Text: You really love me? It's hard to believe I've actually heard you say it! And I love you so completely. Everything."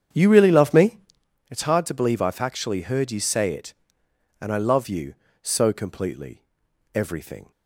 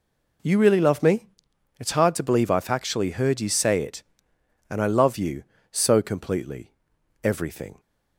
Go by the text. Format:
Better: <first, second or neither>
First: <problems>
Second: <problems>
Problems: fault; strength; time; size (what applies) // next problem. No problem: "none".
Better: second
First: starts louder than the rest; strong; until 1.3 s; 8.5 dB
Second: none